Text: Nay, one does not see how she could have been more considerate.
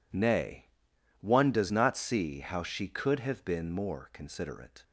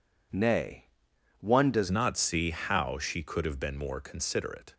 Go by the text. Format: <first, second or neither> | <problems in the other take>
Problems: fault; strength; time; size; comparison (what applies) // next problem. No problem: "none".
first | changes voice at "not"; from 1.8 s on; 2.9 s long